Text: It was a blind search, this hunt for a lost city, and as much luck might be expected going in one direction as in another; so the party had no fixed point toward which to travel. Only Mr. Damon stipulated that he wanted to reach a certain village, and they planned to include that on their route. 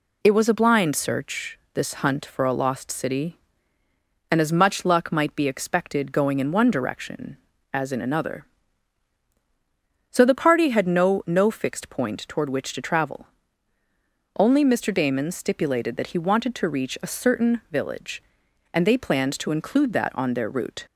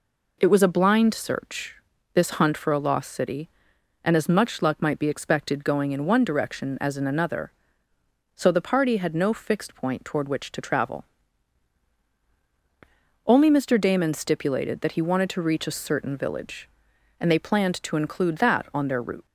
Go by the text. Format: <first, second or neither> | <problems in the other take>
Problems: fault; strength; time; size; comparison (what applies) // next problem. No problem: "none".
second | says "no" twice; at 11.2 s